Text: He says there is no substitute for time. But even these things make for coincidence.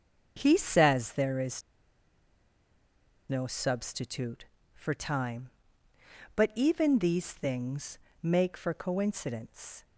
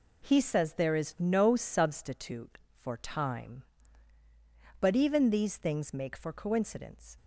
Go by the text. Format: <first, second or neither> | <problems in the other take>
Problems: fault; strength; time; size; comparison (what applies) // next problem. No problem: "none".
second | starts louder than the rest; until 1.3 s; 6.5 dB // pauses between "is" and "no"; strong; at 1.6 s; 1.6 s long // pauses between "things" and "make"; slight; at 7.9 s; 0.24 s long